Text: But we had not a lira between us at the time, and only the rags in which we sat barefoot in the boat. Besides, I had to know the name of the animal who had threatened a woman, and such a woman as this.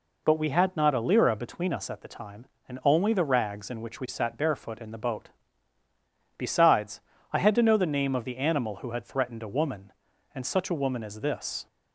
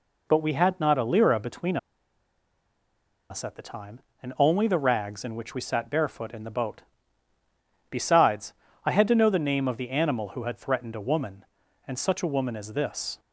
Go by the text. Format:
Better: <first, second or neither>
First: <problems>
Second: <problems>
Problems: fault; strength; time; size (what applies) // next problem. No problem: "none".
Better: first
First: none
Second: pauses between "between" and "us"; strong; at 1.7 s; 1.5 s long